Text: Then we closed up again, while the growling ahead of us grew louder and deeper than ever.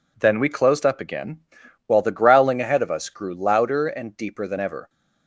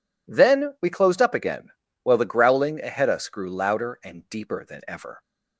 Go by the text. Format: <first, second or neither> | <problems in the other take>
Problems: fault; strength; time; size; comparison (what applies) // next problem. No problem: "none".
first | skips "of"; at 3.1 s